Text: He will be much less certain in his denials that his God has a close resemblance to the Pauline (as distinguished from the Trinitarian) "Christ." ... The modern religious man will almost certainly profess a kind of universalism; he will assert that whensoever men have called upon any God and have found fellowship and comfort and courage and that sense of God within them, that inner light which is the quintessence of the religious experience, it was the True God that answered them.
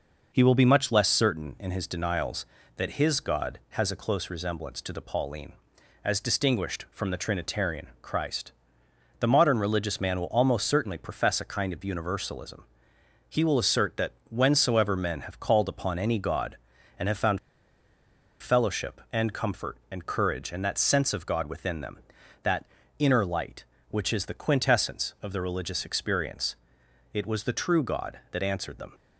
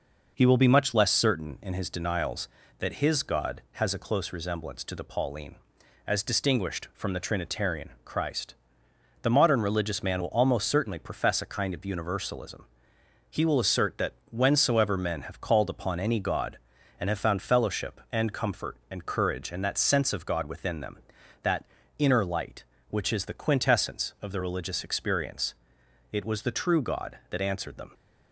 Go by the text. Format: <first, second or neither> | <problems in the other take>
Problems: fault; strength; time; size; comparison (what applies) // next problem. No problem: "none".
second | pauses between "that" and "whensoever"; slight; at 14.1 s; 0.18 s long; slight in the second // pauses between "found" and "fellowship"; at 17.3 s; 1.0 s long // pauses between "that" and "inner"; slight; at 22.6 s; 0.32 s long; slight in the second